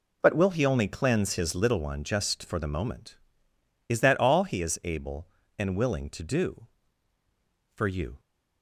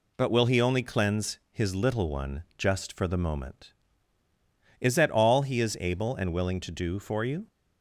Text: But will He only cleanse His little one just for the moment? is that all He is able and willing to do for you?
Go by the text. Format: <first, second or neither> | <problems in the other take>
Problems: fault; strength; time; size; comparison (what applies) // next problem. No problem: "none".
neither | none